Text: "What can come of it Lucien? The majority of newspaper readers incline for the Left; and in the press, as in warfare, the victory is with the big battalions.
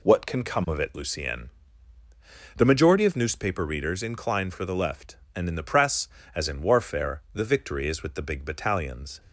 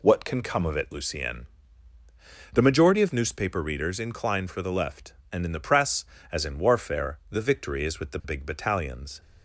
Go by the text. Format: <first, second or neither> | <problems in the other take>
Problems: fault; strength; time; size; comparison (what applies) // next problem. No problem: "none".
neither | none